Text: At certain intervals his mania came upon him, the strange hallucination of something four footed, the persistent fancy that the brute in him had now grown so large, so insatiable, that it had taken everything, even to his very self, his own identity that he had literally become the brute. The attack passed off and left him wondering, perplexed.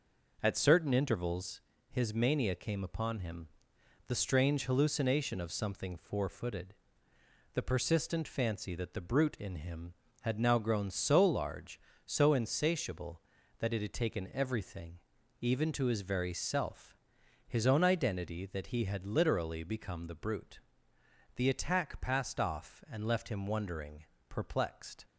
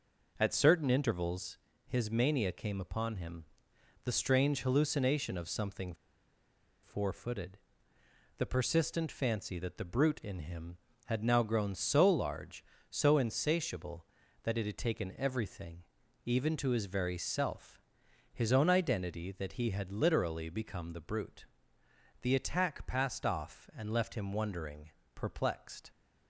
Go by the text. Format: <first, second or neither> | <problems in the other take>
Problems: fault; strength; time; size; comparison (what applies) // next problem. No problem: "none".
first | pauses between "intervals" and "his"; slight; at 1.5 s; 0.30 s long; slight in the first // pauses between "something" and "four"; noticeable; at 5.9 s; 0.89 s long